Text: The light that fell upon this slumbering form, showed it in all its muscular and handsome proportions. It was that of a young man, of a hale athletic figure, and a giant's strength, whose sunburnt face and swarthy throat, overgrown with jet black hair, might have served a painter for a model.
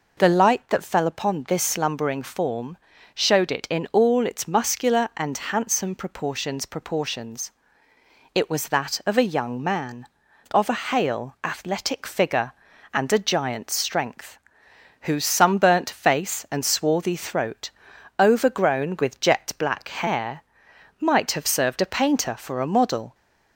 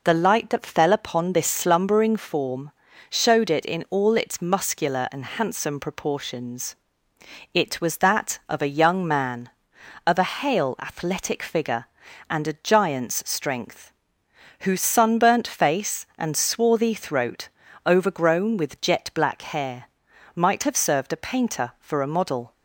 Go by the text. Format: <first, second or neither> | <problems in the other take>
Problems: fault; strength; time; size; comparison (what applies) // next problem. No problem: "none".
second | says "proportions" twice; at 6.6 s